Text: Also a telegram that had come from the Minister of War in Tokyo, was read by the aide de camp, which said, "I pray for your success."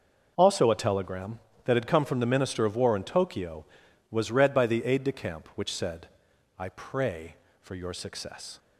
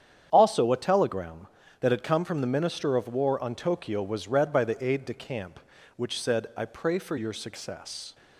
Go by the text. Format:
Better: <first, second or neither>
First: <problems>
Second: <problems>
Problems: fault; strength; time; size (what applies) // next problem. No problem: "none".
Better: first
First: none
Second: starts louder than the rest; strong; until 1.3 s; 8.5 dB // says "on" for "in"; at 3.4 s